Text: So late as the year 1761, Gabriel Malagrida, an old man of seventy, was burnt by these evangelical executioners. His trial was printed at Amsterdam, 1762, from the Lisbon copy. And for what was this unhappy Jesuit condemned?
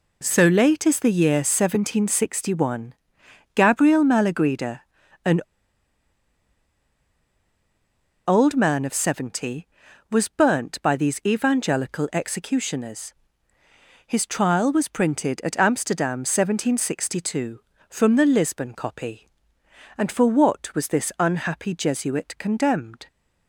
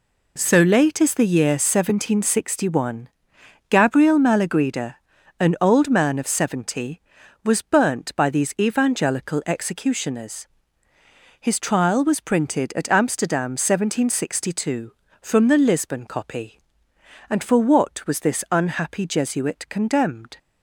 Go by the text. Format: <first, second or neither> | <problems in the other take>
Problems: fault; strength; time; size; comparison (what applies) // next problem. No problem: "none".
second | pauses between "an" and "old"; strong; at 5.3 s; 2.8 s long